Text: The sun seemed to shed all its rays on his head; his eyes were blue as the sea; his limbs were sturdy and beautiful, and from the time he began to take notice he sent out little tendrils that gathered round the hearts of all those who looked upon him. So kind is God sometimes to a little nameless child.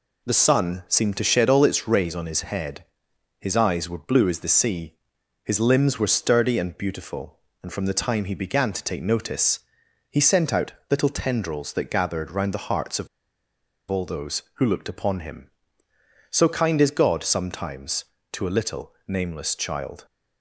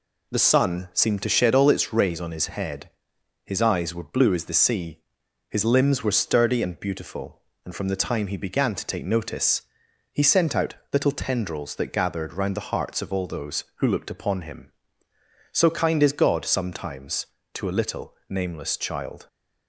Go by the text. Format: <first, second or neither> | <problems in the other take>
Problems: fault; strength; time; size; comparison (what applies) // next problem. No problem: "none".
second | pauses between "notice" and "he"; noticeable; at 9.6 s; 0.50 s long; noticeable in the second // pauses between "out" and "little"; slight; at 10.7 s; 0.18 s long; slight in the second // pauses between "of" and "all"; noticeable; at 13.0 s; 0.81 s long // pauses between "little" and "nameless"; slight; at 18.9 s; 0.16 s long; slight in the second